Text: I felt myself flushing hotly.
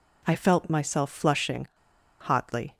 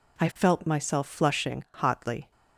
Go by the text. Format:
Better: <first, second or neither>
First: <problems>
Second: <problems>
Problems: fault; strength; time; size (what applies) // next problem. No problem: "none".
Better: second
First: pauses between "flushing" and "hotly"; noticeable; at 1.6 s; 0.53 s long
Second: none